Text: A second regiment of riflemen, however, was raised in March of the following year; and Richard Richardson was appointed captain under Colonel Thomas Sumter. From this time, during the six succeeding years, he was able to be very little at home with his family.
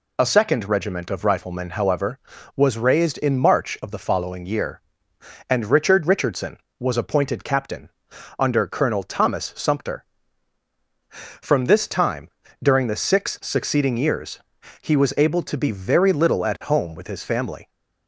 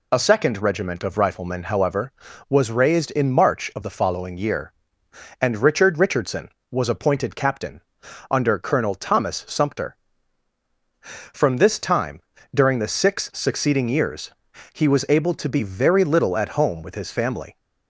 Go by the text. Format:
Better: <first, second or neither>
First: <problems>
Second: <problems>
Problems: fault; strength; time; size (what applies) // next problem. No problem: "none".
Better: neither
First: pauses between "captain" and "under"; noticeable; at 7.8 s; 0.48 s long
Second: pauses between "captain" and "under"; noticeable; at 7.8 s; 0.48 s long